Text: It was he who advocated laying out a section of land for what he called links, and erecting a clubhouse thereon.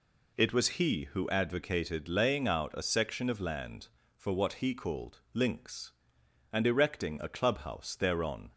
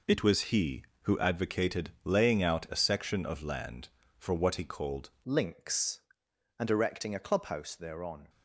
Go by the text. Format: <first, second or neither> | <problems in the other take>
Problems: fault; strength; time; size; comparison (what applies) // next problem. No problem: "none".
first | changes voice at "links"; from 5.2 s on; 3.0 s long